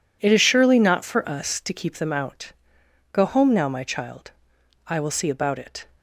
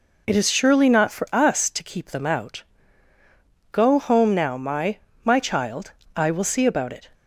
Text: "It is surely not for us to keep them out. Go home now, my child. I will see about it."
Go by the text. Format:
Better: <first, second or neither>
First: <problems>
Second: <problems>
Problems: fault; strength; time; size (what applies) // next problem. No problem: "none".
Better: first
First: none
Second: says "my" twice; at 5.2 s